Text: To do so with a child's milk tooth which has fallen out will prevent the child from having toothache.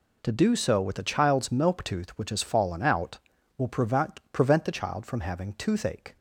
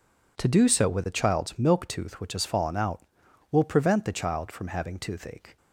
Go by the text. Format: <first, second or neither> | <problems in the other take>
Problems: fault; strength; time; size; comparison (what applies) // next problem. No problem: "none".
second | says "prevent" twice; at 4.3 s